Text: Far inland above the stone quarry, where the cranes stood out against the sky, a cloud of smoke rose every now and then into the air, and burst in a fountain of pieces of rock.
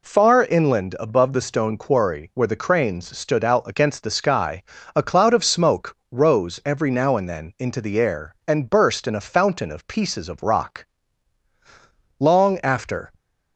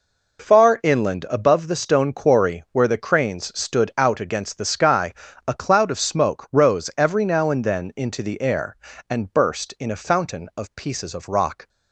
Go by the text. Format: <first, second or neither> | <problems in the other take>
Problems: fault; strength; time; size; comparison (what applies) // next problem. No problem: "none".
second | goes on to say "Long after"; noticeable; from 12.2 s on; 0.92 s long